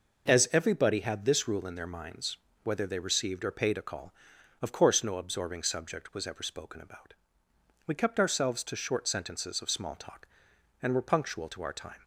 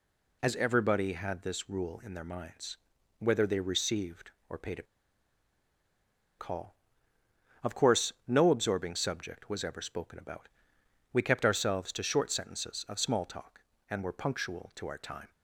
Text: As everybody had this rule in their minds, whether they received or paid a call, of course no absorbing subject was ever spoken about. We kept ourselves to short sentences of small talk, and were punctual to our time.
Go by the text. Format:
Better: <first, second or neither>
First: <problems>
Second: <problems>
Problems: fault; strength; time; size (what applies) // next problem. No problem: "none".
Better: first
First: none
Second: pauses between "a" and "call"; strong; at 4.8 s; 1.5 s long